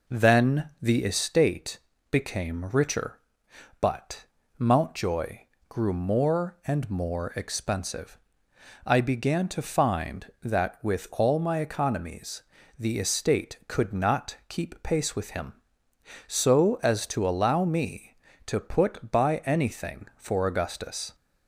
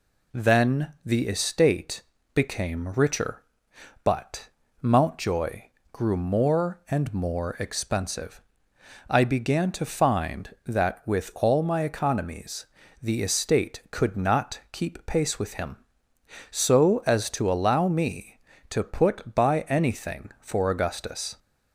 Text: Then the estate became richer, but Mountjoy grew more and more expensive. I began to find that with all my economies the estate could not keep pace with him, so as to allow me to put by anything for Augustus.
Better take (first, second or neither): second